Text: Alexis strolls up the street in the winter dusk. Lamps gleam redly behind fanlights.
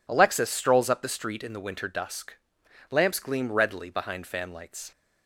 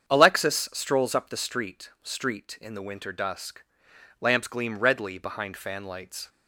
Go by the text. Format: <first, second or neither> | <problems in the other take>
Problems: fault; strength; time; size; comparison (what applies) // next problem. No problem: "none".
first | starts louder than the rest; strong; until 1.1 s; 7.5 dB // says "street" twice; at 2.0 s